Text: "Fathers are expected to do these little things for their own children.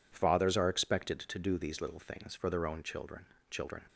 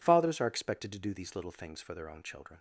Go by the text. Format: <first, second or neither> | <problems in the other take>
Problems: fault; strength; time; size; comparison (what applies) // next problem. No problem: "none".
second | says "children" twice; at 3.4 s